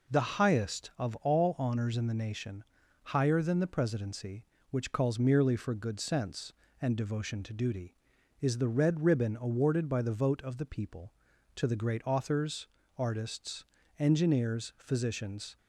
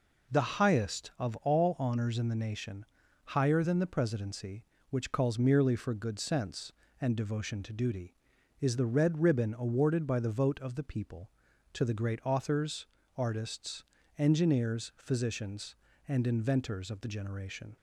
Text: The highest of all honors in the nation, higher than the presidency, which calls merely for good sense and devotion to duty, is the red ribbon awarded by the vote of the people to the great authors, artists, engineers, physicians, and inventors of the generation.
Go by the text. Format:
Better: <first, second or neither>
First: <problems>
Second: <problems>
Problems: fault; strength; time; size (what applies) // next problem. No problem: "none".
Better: second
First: stops before "and inventors of the generation"; at 15.5 s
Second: none